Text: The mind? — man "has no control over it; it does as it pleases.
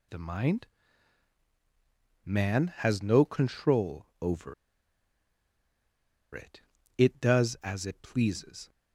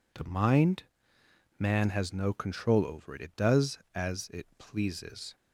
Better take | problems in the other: second | pauses between "control" and "over"; slight; at 4.0 s; 0.16 s long // pauses between "over" and "it"; strong; at 4.5 s; 1.8 s long

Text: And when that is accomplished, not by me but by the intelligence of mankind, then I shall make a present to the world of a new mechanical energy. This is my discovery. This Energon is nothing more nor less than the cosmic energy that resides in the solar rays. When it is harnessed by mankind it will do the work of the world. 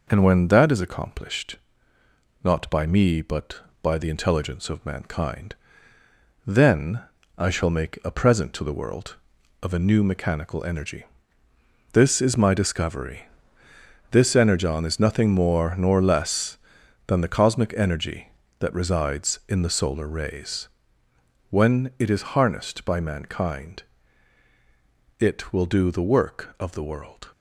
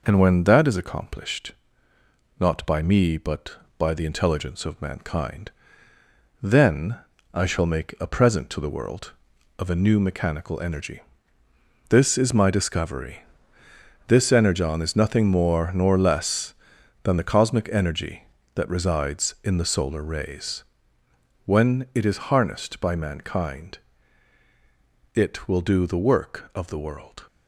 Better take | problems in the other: neither | pauses between "then" and "I"; slight; the same in both // pauses between "mankind" and "it"; strong; the same in both

